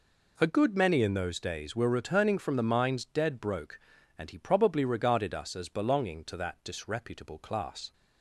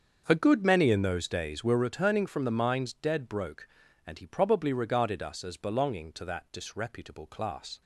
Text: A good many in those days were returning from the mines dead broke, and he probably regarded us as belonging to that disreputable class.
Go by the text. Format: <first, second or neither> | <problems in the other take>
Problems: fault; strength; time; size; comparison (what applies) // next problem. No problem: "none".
first | starts louder than the rest; until 1.9 s; 7 dB